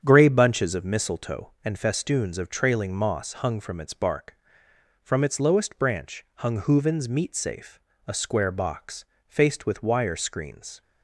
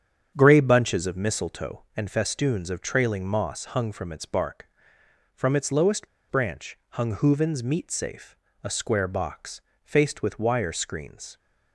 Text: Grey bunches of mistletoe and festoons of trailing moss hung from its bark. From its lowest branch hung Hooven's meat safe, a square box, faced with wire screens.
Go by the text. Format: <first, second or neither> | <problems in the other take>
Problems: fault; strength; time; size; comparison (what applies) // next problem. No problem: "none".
first | starts louder than the rest; strong; until 1.3 s; 8.5 dB; strong in the first // pauses between "lowest" and "branch"; slight; at 6.0 s; 0.21 s long